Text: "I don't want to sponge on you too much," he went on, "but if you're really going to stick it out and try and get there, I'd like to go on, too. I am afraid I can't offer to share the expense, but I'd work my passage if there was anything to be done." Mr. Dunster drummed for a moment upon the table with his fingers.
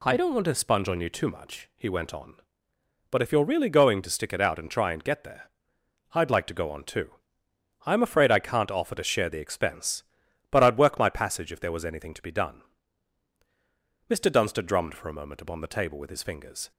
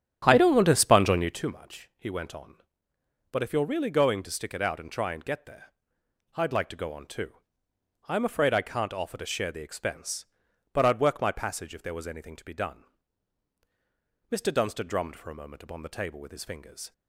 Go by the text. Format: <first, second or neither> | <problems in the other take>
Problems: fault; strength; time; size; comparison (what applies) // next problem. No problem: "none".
first | starts louder than the rest; strong; until 1.5 s; 9.5 dB